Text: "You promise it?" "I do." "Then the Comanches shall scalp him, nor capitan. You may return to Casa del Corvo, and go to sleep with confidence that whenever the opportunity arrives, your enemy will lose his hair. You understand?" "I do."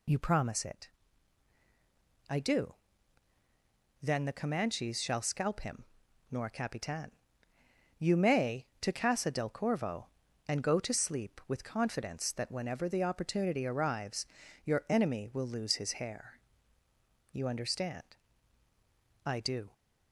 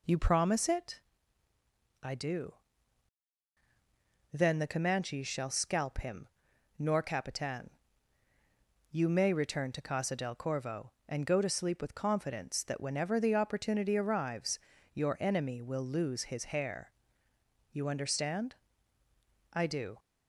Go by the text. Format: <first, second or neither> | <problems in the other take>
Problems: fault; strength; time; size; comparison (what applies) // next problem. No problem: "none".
second | skips "return"; at 8.7 s